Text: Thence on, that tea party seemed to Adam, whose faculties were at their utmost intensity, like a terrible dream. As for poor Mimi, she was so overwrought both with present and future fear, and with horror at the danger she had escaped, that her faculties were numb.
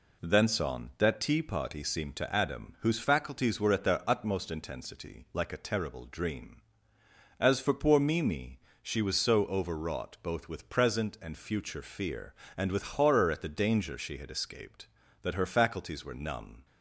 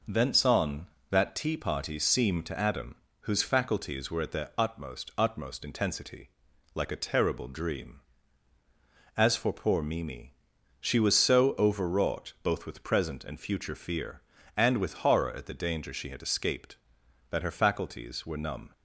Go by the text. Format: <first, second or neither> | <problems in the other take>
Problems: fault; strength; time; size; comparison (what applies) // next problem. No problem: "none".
first | says "utmost" twice; at 5.1 s